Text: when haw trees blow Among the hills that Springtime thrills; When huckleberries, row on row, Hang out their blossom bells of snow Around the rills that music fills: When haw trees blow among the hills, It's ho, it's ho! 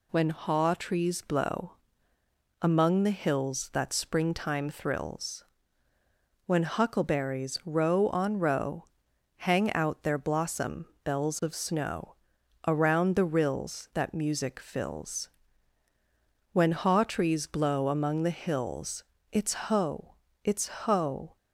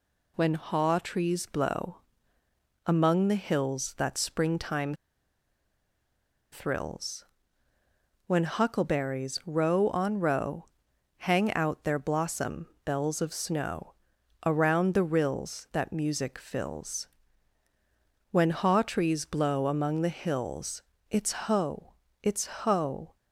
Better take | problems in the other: first | pauses between "blow" and "Among"; noticeable; at 2.0 s; 0.84 s long; noticeable in the first // pauses between "Springtime" and "thrills"; strong; at 4.9 s; 1.5 s long // pauses between "blossom" and "bells"; slight; at 12.6 s; 0.18 s long; slight in the first // pauses between "snow" and "Around"; noticeable; at 13.9 s; 0.52 s long; noticeable in the first

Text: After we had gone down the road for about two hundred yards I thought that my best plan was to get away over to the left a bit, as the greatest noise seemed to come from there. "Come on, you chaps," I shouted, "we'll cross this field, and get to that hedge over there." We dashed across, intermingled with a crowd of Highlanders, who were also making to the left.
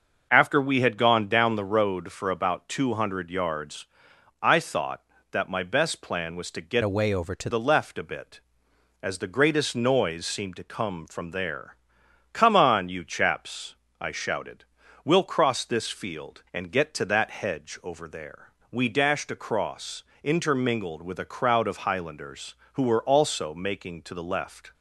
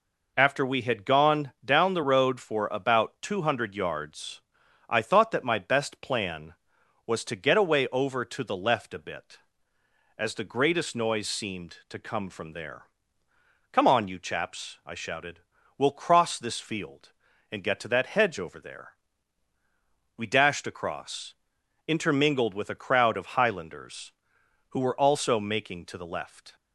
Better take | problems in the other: second | starts louder than the rest; noticeable; until 1.3 s; 6 dB // pauses between "yards" and "I"; noticeable; at 3.8 s; 0.58 s long; noticeable in the second // changes voice from "away" to "to"; from 6.8 to 7.4 s; 0.6 s long

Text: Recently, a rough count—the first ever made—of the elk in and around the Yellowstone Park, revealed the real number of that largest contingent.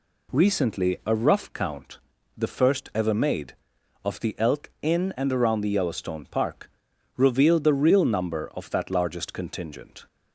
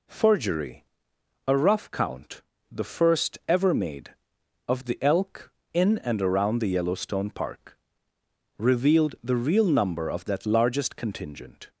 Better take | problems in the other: first | says "Forgery" for "Recently"; at 0.0 s

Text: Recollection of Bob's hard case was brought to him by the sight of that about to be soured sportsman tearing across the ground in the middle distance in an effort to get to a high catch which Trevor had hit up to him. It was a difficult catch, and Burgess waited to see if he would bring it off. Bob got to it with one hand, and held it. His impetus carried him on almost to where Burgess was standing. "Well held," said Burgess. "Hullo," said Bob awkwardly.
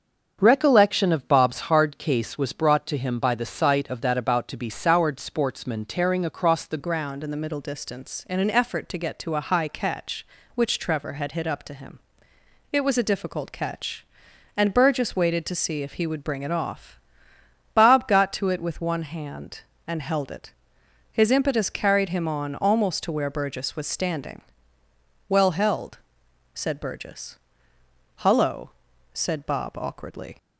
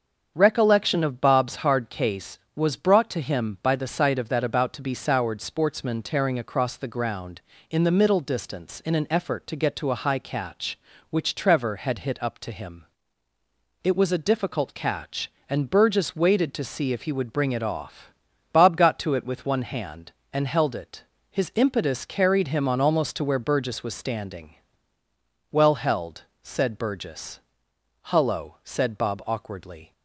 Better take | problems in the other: second | starts louder than the rest; strong; until 1.4 s; 7.5 dB; strong in the second // changes voice at "ground"; from 6.7 s on; 23.6 s long

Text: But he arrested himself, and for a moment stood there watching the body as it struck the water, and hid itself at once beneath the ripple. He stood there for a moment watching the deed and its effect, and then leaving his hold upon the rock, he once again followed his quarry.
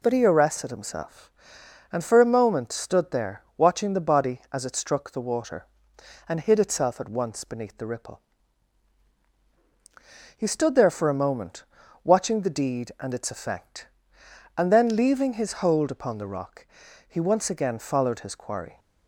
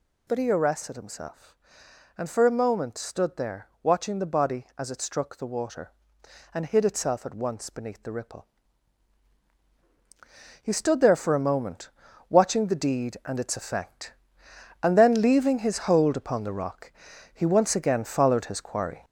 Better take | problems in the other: first | gets louder; noticeable; throughout; 4.5 dB // pauses between "there" and "watching"; slight; at 3.6 s; 0.16 s long; slight in the first // pauses between "moment" and "watching"; at 11.8 s; 0.40 s long; also in the first

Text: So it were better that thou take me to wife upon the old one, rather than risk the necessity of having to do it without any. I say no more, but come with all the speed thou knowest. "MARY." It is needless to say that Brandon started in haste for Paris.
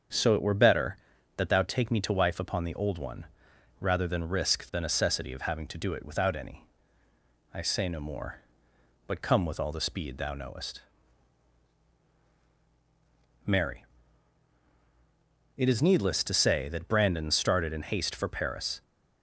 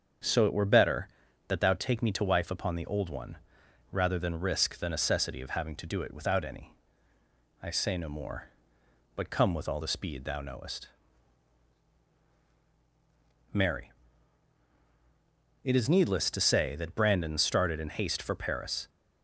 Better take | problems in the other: neither | starts louder than the rest; strong; the same in both

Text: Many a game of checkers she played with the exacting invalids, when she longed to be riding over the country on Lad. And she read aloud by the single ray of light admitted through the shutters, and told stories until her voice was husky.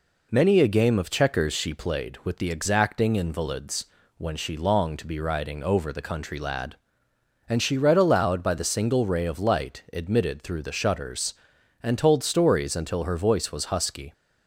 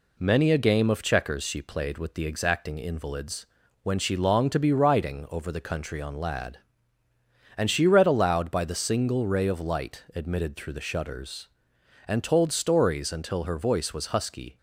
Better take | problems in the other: second | skips "on"; at 6.3 s

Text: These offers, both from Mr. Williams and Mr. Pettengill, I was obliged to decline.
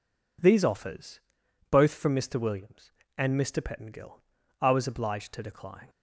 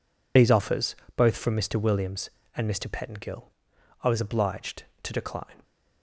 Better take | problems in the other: first | loses the start of "These"; at 0.3 s; 50 ms

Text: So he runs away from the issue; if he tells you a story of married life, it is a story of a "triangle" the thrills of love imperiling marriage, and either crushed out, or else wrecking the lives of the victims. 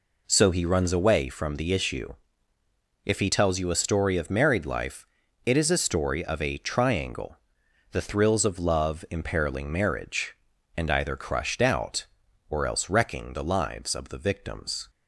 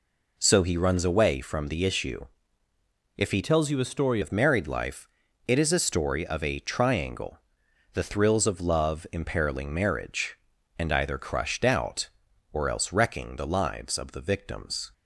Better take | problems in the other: first | changes voice from "tells" to "story"; from 3.4 to 4.2 s; 0.8 s long // pauses between "triangle" and "the"; noticeable; at 7.4 s; 0.52 s long; noticeable in the first

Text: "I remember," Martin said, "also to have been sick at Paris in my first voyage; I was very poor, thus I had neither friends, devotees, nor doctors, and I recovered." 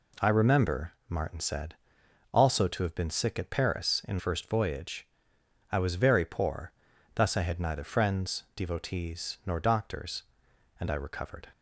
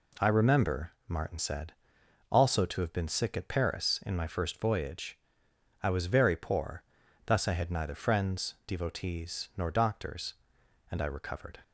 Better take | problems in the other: second | skips "my"; at 4.1 s

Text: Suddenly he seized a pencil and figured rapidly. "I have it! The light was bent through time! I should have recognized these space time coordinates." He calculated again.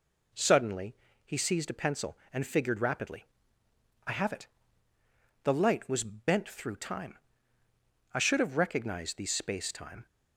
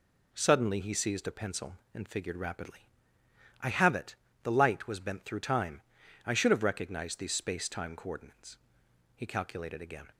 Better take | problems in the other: second | pauses between "Suddenly" and "he"; slight; at 0.9 s; 0.30 s long // stops before "coordinates He calculated again"; at 10.0 s

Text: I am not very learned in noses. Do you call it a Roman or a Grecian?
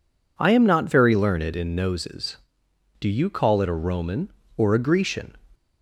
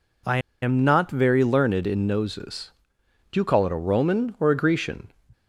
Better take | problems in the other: first | pauses between "I" and "am"; slight; at 0.3 s; 0.23 s long

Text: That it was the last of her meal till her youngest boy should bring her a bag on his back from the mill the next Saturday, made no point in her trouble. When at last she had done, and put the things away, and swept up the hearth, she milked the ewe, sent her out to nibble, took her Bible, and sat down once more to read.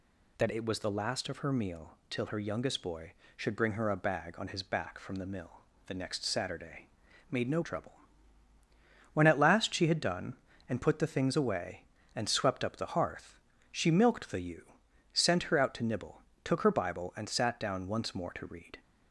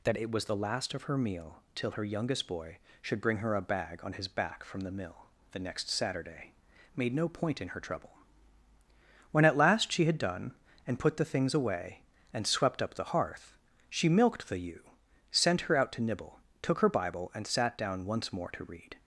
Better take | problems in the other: second | pauses between "mill" and "the"; slight; at 5.6 s; 0.26 s long; slight in the second // skips "point in her"; at 7.6 s

